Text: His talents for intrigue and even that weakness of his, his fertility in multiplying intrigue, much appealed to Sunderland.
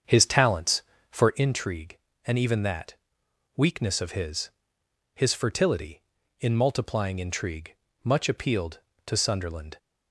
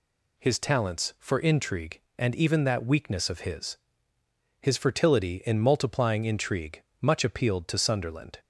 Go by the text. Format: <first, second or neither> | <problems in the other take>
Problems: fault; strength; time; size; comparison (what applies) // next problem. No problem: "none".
second | starts louder than the rest; strong; until 1.4 s; 7 dB // pauses between "that" and "weakness"; noticeable; at 2.9 s; 0.62 s long